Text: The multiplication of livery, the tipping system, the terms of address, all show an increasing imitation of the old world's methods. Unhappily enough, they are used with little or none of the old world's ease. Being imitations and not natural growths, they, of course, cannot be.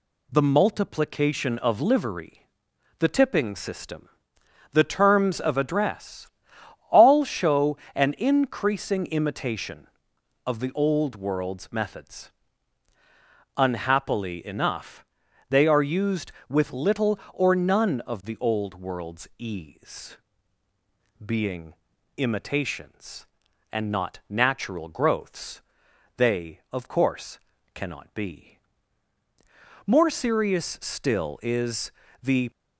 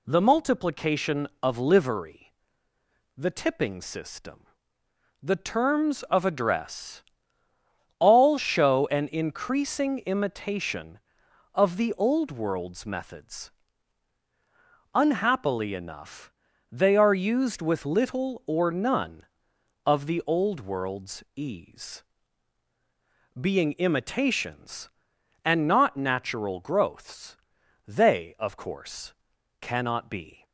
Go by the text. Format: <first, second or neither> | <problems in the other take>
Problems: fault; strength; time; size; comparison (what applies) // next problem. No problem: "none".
second | pauses between "show" and "an"; slight; at 7.7 s; 0.18 s long // pauses between "Being" and "imitations"; at 21.7 s; 0.42 s long // goes on to say "More serious still is the"; strong; from 29.8 s on; 2.6 s long